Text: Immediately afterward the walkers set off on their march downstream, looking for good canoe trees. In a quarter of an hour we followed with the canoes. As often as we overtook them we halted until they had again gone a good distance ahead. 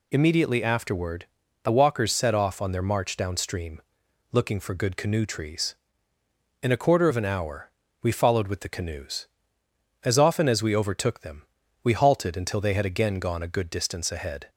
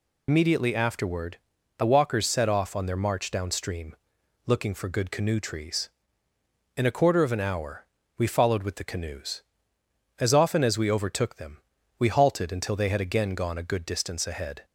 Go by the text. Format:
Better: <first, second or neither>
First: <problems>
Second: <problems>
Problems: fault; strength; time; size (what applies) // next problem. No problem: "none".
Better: first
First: pauses between "afterward" and "the"; slight; at 1.2 s; 0.36 s long // pauses between "hour" and "we"; slight; at 7.7 s; 0.30 s long // pauses between "them" and "we"; at 11.4 s; 0.40 s long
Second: loses the start of "Immediately"; at 0.2 s; 60 ms // pauses between "afterward" and "the"; at 1.3 s; 0.38 s long // pauses between "hour" and "we"; slight; at 7.8 s; 0.30 s long // pauses between "them" and "we"; at 11.5 s; 0.40 s long